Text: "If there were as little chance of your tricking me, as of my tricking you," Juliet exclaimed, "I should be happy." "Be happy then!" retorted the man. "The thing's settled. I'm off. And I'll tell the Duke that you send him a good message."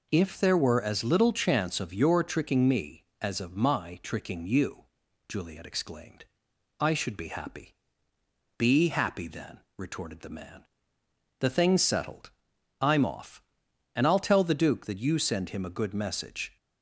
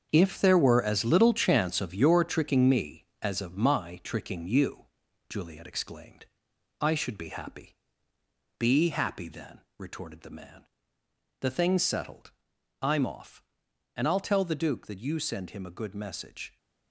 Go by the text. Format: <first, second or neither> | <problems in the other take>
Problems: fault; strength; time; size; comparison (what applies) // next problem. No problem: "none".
first | gets quieter; strong; throughout; 10.5 dB